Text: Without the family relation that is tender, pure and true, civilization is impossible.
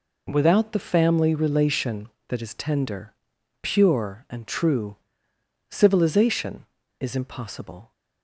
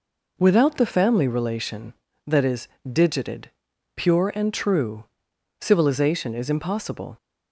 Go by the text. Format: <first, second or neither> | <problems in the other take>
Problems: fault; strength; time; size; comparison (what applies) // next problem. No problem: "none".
first | says "digited" for "tender"; at 2.9 s